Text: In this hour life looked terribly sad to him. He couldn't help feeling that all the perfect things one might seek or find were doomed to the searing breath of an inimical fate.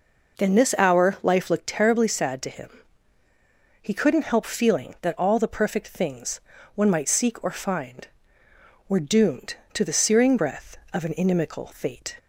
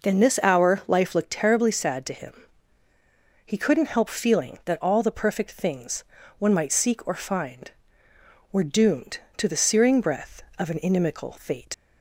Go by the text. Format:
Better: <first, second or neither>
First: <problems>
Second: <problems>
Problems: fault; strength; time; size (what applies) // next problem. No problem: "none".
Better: first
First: pauses between "things" and "one"; slight; at 6.4 s; 0.34 s long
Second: pauses between "things" and "one"; slight; at 6.0 s; 0.34 s long // leaves "fate" unfinished; at 11.7 s; 95 ms